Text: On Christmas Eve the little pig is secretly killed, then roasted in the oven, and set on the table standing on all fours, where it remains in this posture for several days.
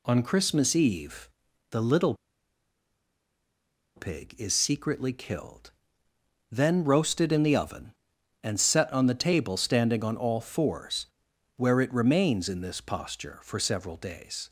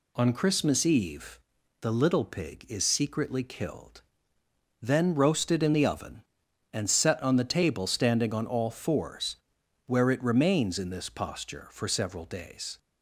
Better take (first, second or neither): second